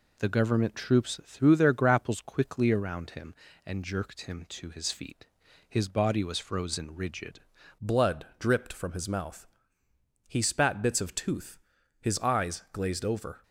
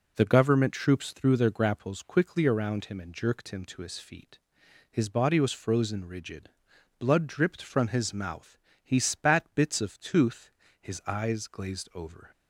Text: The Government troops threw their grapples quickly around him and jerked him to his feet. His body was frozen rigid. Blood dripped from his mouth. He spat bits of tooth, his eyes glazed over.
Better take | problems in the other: second | changes voice at "Blood"; from 7.8 s on; 5.6 s long

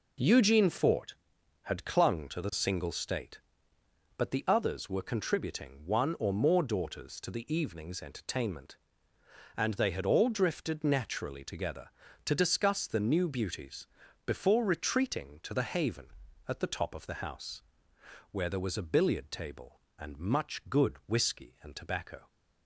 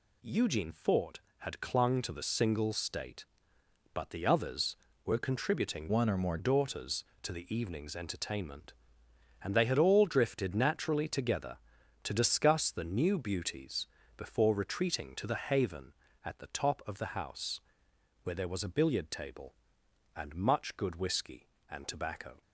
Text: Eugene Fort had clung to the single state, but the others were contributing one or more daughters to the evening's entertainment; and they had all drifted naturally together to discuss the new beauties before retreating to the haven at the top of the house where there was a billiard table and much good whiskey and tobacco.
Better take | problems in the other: first | changes voice from "one" to "more"; from 5.9 to 6.3 s; 0.4 s long // pauses between "beauties" and "before"; slight; at 13.8 s; 0.30 s long; also in the first // pauses between "house" and "where"; noticeable; at 17.6 s; 0.62 s long; noticeable in the first

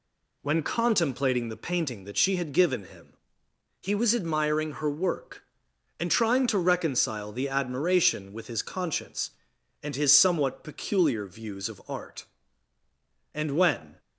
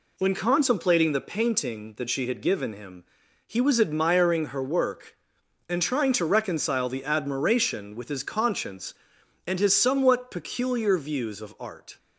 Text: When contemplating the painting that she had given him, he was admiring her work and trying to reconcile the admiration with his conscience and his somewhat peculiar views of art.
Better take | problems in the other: second | goes on to say "And when"; noticeable; from 13.3 s on; 0.66 s long

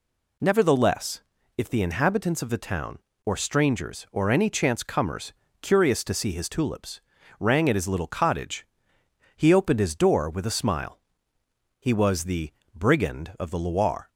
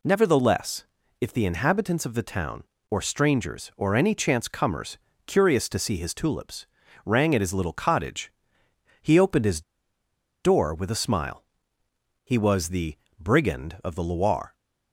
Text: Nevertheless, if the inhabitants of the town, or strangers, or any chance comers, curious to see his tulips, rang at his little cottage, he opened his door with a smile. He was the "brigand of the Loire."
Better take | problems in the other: first | pauses between "his" and "door"; noticeable; at 9.6 s; 0.81 s long // pauses between "the" and "brigand"; slight; at 12.9 s; 0.22 s long; slight in the first

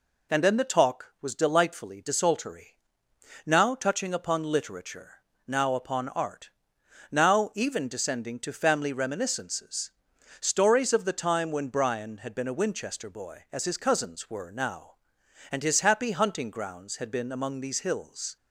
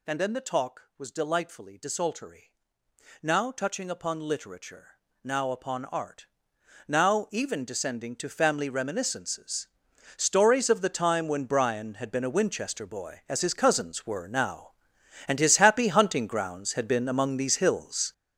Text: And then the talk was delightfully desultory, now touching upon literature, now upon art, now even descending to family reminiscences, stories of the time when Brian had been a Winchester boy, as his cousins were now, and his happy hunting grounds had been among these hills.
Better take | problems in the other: first | gets louder; strong; throughout; 10 dB

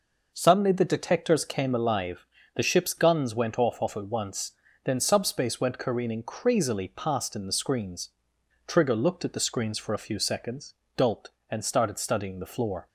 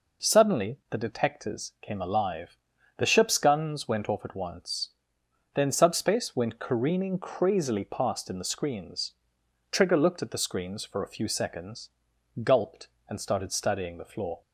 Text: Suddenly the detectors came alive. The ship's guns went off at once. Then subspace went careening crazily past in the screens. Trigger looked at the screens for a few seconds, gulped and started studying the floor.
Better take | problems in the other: second | says "off" twice; at 3.7 s

